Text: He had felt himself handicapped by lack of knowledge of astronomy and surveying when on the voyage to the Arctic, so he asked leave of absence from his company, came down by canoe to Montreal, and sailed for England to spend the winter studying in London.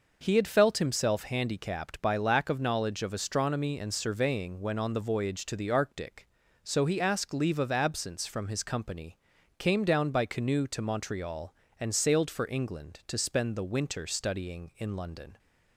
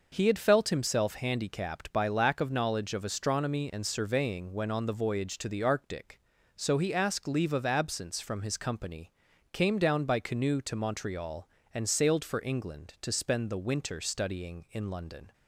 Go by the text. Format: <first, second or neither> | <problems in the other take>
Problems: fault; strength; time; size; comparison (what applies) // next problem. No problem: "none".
neither | none